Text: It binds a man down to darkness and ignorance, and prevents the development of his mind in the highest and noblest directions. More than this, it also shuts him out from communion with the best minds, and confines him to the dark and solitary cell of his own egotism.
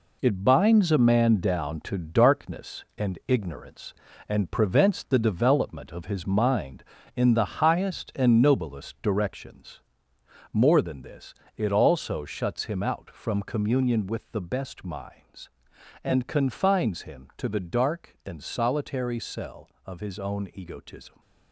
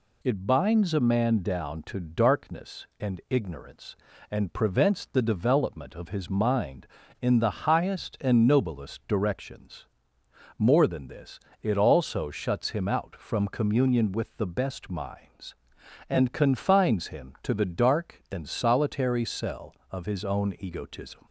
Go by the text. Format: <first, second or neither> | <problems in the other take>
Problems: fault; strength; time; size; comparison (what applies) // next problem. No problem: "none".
second | gets quieter; strong; throughout; 8.5 dB